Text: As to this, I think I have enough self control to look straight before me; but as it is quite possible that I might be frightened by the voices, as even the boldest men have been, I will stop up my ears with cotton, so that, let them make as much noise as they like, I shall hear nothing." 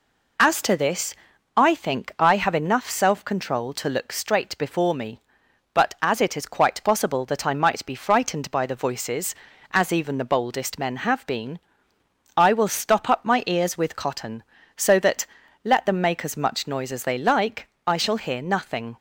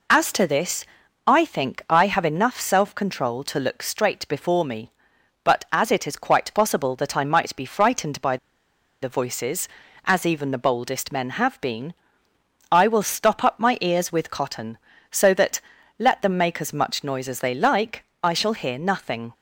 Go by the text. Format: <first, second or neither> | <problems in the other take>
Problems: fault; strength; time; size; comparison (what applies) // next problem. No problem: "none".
first | pauses between "by" and "the"; noticeable; at 8.3 s; 0.66 s long